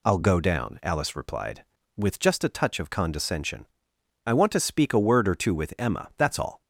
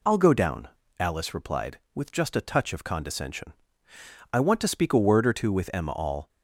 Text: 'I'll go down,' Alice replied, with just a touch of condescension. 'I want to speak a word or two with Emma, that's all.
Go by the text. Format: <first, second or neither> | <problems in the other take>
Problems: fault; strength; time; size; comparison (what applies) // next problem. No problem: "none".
first | skips "that's"; at 5.9 s